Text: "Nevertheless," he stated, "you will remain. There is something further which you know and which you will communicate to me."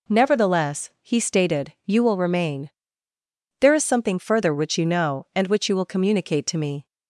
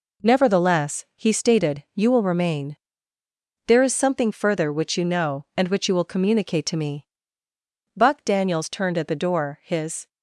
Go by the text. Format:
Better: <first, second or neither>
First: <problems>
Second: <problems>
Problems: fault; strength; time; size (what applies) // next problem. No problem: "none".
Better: first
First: none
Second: goes on to say "Buck Daniels turned at the door his"; strong; from 7.9 s on; 2.1 s long